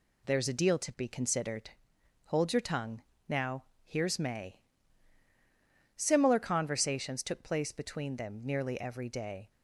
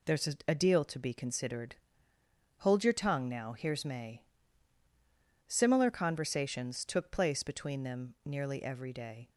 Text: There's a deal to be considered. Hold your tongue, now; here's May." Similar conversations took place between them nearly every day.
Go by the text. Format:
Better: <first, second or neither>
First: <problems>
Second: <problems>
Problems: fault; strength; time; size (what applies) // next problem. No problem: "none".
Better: first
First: none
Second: says "a" twice; at 0.4 s